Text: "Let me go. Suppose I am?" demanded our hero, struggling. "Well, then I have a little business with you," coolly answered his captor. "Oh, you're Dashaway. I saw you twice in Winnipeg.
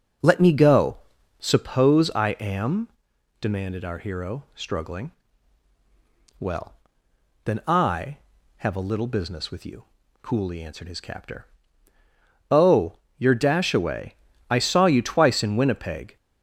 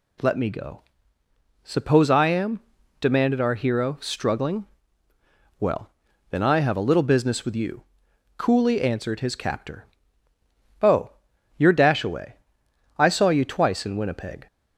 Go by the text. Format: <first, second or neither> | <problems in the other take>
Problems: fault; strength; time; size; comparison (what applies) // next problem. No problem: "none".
second | starts louder than the rest; noticeable; until 1.7 s; 6 dB